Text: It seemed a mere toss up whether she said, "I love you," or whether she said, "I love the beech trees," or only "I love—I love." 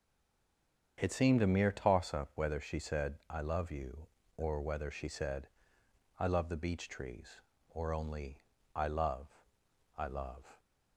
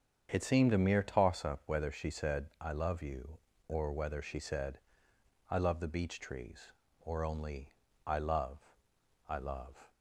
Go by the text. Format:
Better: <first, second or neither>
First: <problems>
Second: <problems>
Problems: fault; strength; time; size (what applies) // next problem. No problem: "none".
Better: second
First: stays silent before the first word; slight; until 0.9 s; 0.9 s long // starts louder than the rest; strong; until 2.0 s; 7.5 dB // pauses between "only" and "I"; slight; at 8.4 s; 0.34 s long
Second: starts louder than the rest; strong; until 1.3 s; 7.5 dB // pauses between "only" and "I"; slight; at 7.7 s; 0.34 s long